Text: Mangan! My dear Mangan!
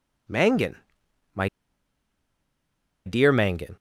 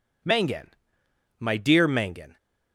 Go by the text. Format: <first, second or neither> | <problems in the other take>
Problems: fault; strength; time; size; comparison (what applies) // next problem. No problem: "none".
second | pauses between "My" and "dear"; strong; at 1.4 s; 1.5 s long